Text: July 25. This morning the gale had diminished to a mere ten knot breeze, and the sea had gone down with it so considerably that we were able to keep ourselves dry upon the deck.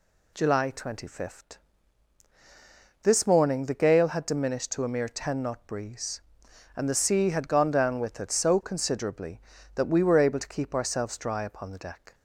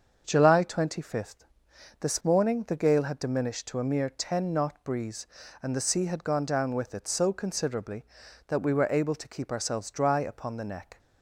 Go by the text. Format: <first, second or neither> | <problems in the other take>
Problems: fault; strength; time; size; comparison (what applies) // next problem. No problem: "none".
first | starts louder than the rest; until 1.2 s; 6.5 dB // says "neck" for "deck"; at 10.6 s